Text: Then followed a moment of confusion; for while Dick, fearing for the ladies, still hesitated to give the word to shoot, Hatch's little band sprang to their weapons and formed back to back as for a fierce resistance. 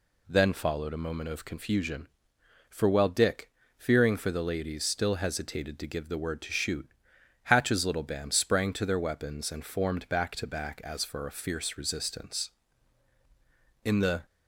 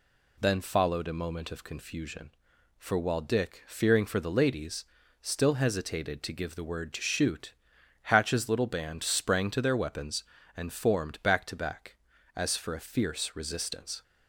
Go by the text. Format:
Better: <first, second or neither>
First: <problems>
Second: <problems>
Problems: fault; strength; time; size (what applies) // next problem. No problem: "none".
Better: second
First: goes on to say "In the"; slight; from 13.8 s on; 0.42 s long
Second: none